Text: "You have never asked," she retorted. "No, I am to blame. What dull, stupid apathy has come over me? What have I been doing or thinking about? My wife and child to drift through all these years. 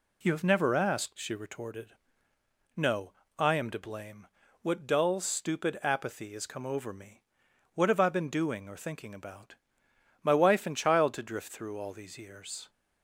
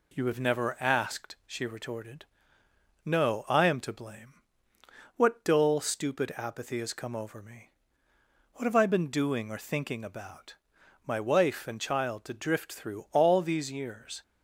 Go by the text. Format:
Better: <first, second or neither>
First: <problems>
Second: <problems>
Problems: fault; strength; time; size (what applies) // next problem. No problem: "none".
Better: neither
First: none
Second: none